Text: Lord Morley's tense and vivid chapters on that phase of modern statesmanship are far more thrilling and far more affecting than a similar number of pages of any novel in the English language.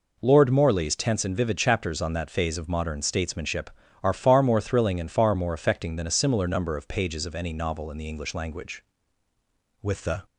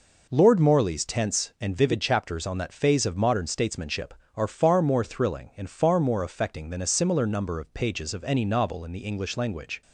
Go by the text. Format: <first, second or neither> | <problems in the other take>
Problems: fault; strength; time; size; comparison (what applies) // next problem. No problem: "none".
second | goes on to say "With the"; slight; from 9.7 s on; 0.44 s long